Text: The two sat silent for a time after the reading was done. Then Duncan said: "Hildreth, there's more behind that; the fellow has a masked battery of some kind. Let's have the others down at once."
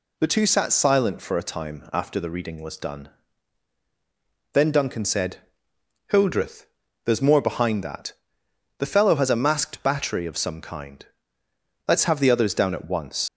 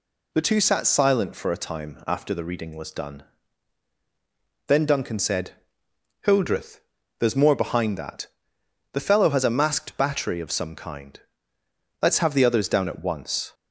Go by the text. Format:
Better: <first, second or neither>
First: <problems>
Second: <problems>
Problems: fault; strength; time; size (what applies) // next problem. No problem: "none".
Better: second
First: leaves "once" unfinished; at 13.2 s; 115 ms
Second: none